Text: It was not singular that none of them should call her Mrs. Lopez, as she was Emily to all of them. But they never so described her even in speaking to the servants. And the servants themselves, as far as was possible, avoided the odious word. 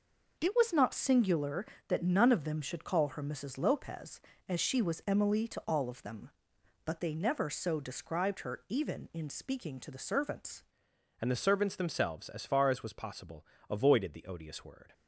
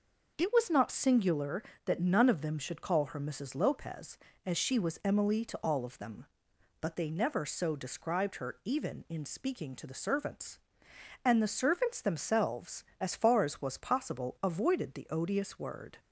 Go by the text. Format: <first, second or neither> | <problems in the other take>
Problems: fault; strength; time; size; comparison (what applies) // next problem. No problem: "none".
second | changes voice at "And"; from 11.2 s on; 3.7 s long